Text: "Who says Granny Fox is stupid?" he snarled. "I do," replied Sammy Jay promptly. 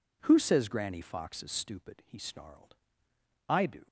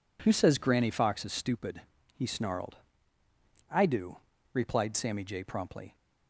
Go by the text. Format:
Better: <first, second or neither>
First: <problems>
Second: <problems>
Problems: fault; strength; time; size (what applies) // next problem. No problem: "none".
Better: second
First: stops before "replied Sammy Jay promptly"; at 3.8 s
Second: none